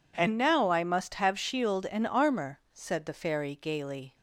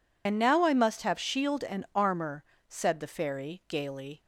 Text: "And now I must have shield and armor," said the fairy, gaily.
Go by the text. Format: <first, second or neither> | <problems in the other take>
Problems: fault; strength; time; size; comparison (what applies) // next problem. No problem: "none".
first | loses the start of "And"; at 0.2 s; 60 ms